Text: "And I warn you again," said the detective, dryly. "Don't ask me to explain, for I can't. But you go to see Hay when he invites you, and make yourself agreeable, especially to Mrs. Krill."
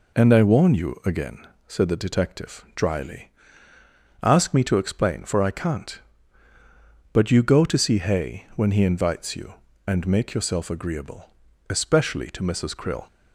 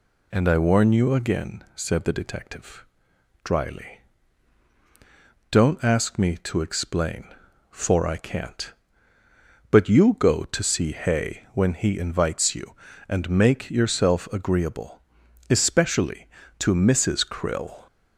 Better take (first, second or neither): second